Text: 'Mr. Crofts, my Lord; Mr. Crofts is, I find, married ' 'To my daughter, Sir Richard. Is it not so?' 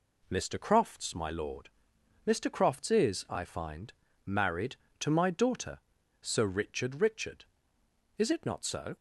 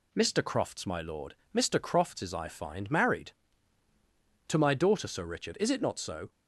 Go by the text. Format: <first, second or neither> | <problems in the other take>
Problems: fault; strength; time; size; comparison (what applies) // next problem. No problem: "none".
second | says "Richard" twice; at 7.0 s